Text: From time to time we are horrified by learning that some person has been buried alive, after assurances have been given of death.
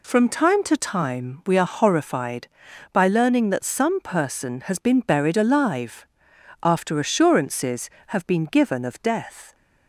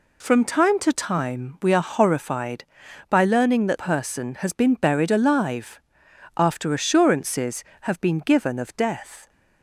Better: first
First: none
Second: skips "some"; at 3.7 s

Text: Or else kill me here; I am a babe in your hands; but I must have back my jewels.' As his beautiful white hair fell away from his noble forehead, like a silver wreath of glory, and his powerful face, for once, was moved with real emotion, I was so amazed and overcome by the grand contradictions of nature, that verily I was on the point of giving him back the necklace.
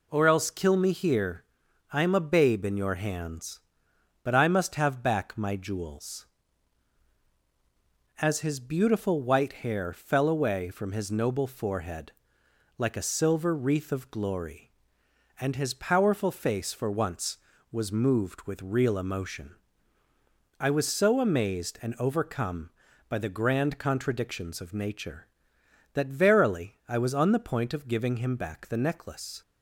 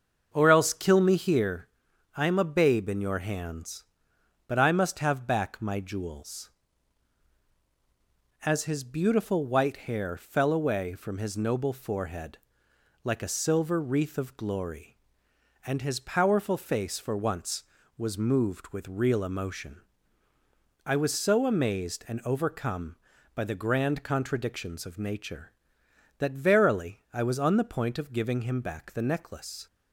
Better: first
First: none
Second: starts louder than the rest; until 1.5 s; 6.5 dB

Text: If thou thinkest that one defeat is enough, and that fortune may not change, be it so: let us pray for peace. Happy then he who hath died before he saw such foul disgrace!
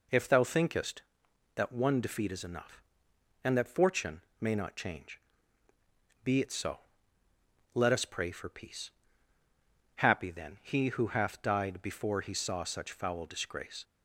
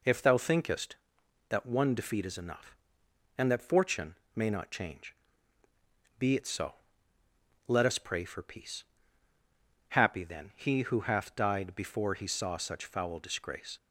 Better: neither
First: pauses between "fortune" and "may"; slight; at 4.2 s; 0.18 s long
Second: pauses between "fortune" and "may"; slight; at 4.1 s; 0.20 s long

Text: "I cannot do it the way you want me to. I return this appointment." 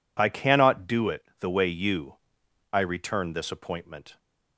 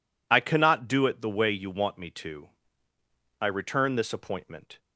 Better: second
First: skips "want me to"; at 2.4 s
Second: none

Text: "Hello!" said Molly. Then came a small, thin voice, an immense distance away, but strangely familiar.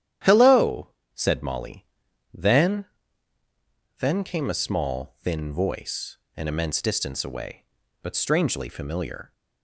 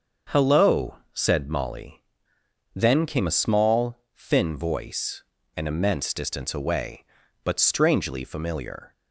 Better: second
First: starts louder than the rest; strong; until 1.5 s; 10.5 dB // says "Then" twice; at 3.9 s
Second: starts louder than the rest; until 1.4 s; 6.5 dB

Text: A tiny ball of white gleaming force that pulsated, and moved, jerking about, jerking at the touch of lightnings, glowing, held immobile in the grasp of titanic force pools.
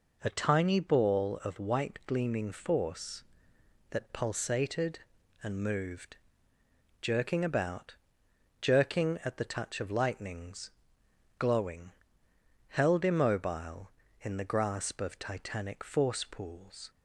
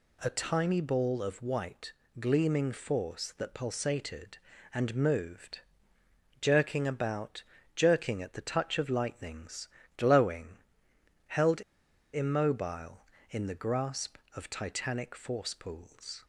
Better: first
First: none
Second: pauses between "white" and "gleaming"; slight; at 1.9 s; 0.26 s long // pauses between "held" and "immobile"; noticeable; at 11.6 s; 0.51 s long

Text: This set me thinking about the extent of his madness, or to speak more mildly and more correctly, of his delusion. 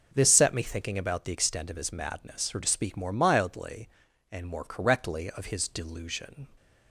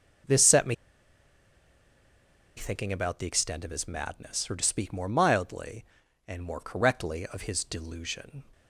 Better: first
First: none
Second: pauses between "me" and "thinking"; strong; at 0.7 s; 1.8 s long

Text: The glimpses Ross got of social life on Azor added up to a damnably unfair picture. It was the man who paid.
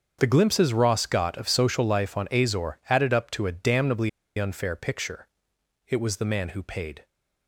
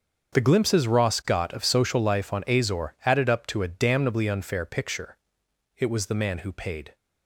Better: second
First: starts louder than the rest; until 1.2 s; 7 dB // pauses between "damnably" and "unfair"; slight; at 4.0 s; 0.28 s long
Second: starts louder than the rest; until 1.3 s; 7 dB

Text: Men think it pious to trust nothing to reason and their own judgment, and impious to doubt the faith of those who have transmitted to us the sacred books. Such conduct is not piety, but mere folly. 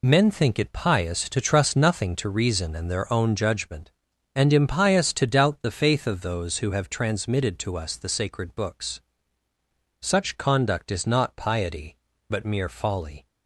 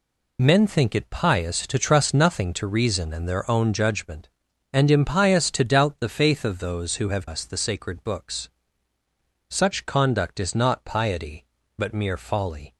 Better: first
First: none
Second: skips "transmitted to"; at 7.2 s

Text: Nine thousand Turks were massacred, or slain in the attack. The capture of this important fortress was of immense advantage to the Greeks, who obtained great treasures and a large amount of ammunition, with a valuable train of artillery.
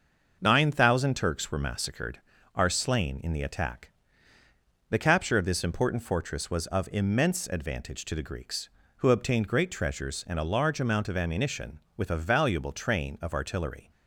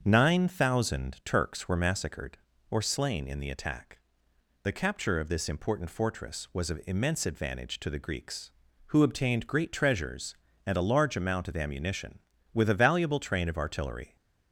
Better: second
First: starts louder than the rest; until 1.4 s; 6.5 dB // says "are" for "or"; at 2.5 s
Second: starts louder than the rest; strong; until 1.0 s; 7 dB

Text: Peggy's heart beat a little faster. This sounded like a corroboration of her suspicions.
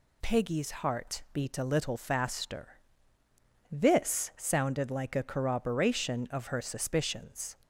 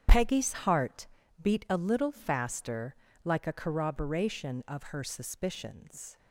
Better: first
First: none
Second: starts louder than the rest; strong; until 1.5 s; 9.5 dB // pauses between "heart" and "beat"; slight; at 1.0 s; 0.34 s long // skips "This sounded"; at 3.0 s

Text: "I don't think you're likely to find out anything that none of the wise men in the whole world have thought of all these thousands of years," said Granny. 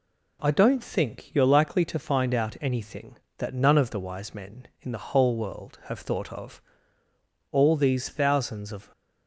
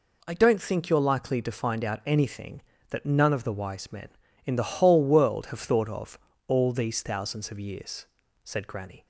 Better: second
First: pauses between "of" and "all"; noticeable; at 6.6 s; 0.90 s long // stops before "years said Granny"; at 8.9 s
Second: pauses between "of" and "all"; slight; at 6.1 s; 0.30 s long

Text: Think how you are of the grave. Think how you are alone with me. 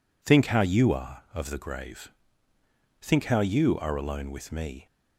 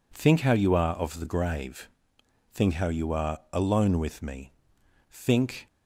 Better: first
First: none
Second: pauses between "are" and "alone"; slight; at 3.3 s; 0.16 s long // goes on to say "Think"; from 5.1 s on; 0.56 s long

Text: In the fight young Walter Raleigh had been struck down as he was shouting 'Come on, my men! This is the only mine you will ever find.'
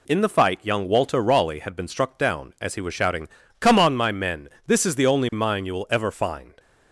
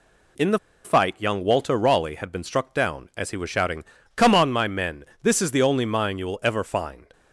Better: first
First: pauses between "shouting" and "Come"; slight; at 3.2 s; 0.30 s long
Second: pauses between "the" and "fight"; slight; at 0.5 s; 0.26 s long // pauses between "shouting" and "Come"; slight; at 3.8 s; 0.30 s long

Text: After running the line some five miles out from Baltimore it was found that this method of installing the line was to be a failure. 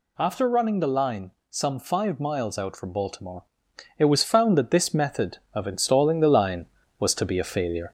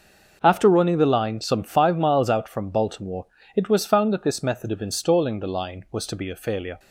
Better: second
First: gets louder; slight; throughout; 2.5 dB // pauses between "line" and "some"; slight; at 1.3 s; 0.18 s long // pauses between "Baltimore" and "it"; noticeable; at 3.4 s; 0.56 s long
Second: pauses between "Baltimore" and "it"; slight; at 3.2 s; 0.32 s long

